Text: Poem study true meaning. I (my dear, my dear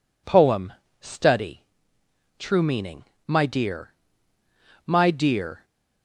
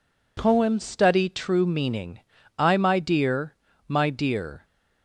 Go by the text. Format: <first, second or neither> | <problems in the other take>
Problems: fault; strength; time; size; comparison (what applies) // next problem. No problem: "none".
second | pauses between "Poem" and "study"; slight; at 0.7 s; 0.28 s long // pauses between "study" and "true"; noticeable; at 1.6 s; 0.76 s long // skips "I"; at 3.1 s